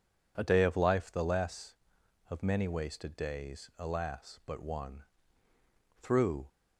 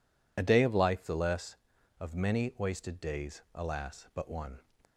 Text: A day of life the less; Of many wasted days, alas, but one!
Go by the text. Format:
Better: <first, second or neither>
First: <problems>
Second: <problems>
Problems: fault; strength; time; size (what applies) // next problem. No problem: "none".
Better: second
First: goes on to say "Through"; slight; from 6.0 s on; 0.46 s long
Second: none